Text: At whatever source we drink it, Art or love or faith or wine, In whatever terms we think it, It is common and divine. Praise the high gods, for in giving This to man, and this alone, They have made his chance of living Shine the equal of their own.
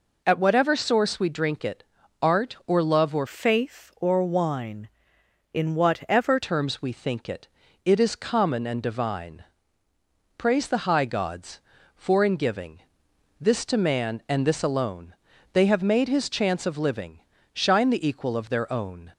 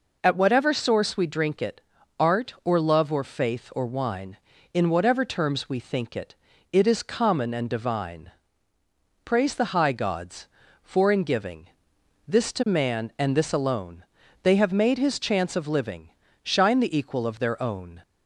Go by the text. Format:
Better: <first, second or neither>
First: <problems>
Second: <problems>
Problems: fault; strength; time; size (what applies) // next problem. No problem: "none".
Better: second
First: changes voice from "faith" to "whatever"; from 3.2 to 6.4 s; 3.2 s long // pauses between "giving" and "This"; noticeable; at 12.8 s; 0.58 s long // pauses between "living" and "Shine"; slight; at 17.1 s; 0.34 s long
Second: pauses between "giving" and "This"; noticeable; at 11.6 s; 0.58 s long // pauses between "living" and "Shine"; slight; at 16.0 s; 0.34 s long